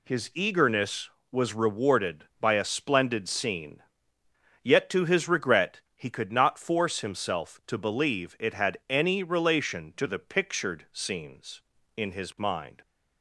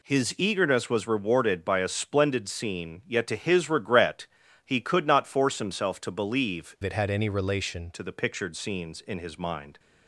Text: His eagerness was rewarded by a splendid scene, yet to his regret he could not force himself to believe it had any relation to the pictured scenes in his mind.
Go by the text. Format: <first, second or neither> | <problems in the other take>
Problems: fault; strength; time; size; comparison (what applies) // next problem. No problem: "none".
first | pauses between "regret" and "he"; at 4.2 s; 0.40 s long; slight in the first // changes voice from "it" to "relation"; from 6.8 to 7.9 s; 1.1 s long